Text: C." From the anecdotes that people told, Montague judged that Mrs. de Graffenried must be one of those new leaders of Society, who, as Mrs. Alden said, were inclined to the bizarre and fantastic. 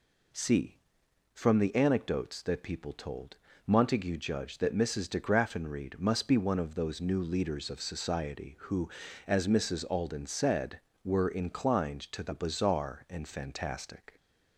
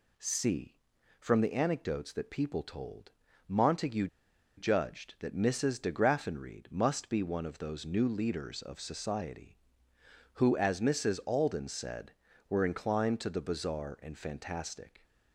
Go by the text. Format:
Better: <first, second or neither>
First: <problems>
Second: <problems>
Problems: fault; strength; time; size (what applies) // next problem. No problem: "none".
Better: first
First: none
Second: pauses between "Montague" and "judged"; noticeable; at 4.0 s; 0.50 s long